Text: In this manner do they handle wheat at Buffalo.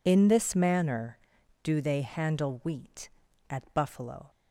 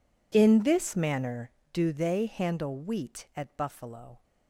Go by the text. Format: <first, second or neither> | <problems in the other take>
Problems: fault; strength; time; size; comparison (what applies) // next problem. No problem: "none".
neither | none